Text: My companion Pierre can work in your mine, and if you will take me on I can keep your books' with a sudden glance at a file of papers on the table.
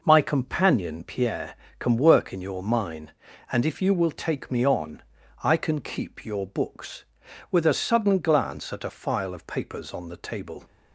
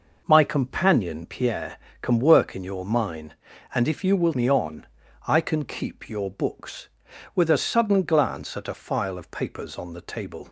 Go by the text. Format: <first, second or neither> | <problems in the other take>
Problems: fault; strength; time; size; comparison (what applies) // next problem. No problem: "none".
first | skips "take"; at 4.3 s // pauses between "on" and "I"; at 4.8 s; 0.40 s long; also in the first